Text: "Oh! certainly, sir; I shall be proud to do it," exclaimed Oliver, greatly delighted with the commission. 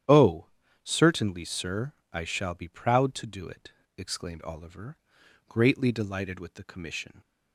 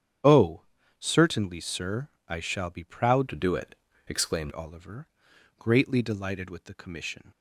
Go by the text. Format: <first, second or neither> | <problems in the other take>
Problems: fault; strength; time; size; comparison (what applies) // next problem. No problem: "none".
first | starts louder than the rest; strong; until 1.5 s; 9 dB; strong in the first // changes voice from "to" to "exclaimed"; from 3.2 to 4.5 s; 1.3 s long